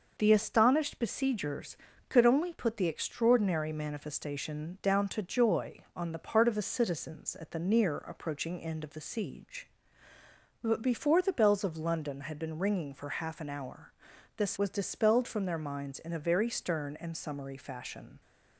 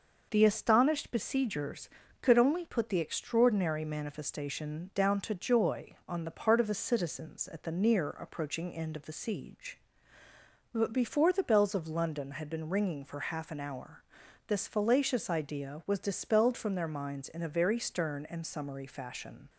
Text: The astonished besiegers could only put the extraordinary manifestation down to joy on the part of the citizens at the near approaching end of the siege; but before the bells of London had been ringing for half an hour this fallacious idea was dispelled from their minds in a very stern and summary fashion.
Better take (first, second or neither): second